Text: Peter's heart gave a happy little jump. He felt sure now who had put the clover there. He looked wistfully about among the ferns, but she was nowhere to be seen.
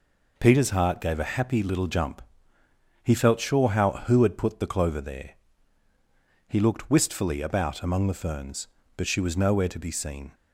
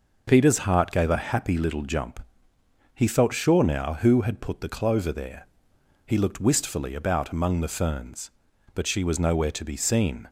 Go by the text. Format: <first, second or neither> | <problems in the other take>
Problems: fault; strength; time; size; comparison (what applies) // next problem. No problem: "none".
second | says "how" for "now"; at 3.6 s